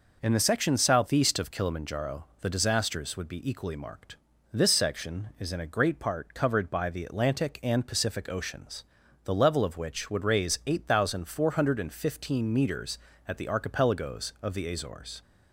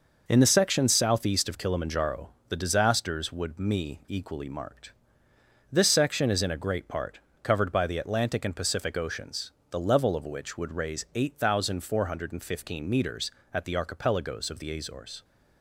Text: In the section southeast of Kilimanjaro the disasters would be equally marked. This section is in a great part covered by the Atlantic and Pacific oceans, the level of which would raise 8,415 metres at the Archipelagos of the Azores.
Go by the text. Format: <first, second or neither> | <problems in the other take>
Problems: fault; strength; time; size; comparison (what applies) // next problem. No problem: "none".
first | pauses between "Kilimanjaro" and "the"; slight; at 2.2 s; 0.18 s long; slight in the first // says "me" for "be"; at 3.5 s // pauses between "part" and "covered"; slight; at 7.1 s; 0.24 s long